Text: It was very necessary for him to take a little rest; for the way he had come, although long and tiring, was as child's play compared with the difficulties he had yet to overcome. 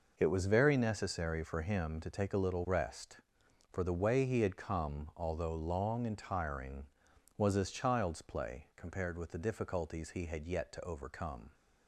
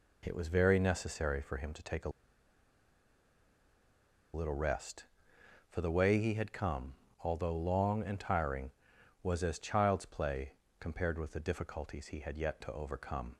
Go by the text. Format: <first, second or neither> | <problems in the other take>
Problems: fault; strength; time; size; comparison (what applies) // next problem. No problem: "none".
first | pauses between "a" and "little"; strong; at 2.0 s; 2.2 s long // pauses between "play" and "compared"; slight; at 10.5 s; 0.26 s long